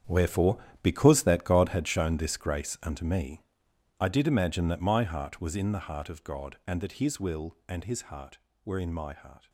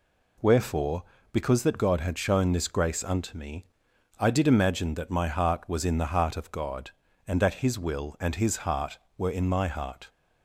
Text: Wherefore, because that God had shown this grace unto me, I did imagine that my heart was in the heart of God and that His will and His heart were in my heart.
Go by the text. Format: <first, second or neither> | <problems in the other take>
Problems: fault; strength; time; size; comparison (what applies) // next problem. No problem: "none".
second | gets quieter; strong; throughout; 14 dB